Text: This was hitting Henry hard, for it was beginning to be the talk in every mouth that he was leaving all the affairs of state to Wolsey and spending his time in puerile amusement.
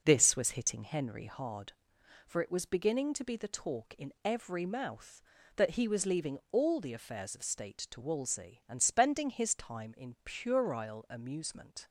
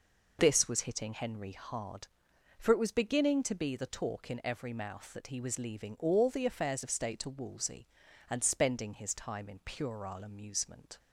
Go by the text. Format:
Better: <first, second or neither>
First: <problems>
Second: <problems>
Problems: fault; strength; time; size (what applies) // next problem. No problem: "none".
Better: neither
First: none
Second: none